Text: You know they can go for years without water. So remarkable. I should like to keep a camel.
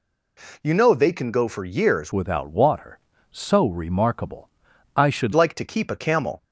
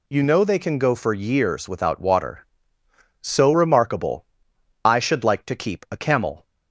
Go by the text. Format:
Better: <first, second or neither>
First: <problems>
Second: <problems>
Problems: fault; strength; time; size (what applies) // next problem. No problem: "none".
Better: second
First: changes voice from "without" to "should"; from 2.1 to 5.3 s; 3.2 s long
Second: none